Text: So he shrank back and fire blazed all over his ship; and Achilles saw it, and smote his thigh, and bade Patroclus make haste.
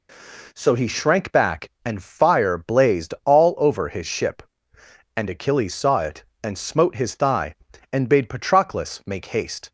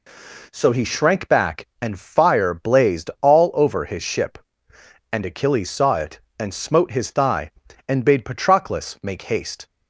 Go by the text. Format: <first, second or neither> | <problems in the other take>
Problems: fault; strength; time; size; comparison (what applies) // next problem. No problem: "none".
neither | none